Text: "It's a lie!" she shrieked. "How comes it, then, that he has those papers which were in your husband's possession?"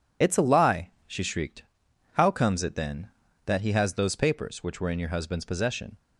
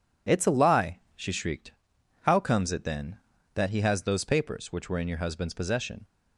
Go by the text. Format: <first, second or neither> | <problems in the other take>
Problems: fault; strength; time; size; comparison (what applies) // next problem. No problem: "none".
second | loses the start of "It's"; at 0.2 s; 30 ms